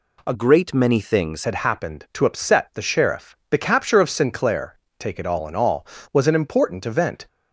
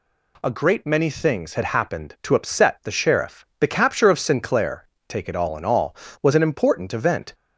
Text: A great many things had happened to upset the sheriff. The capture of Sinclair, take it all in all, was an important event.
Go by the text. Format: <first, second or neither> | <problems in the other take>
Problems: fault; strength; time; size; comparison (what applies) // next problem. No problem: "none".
second | changes voice from "great" to "things"; from 0.3 to 1.4 s; 1.1 s long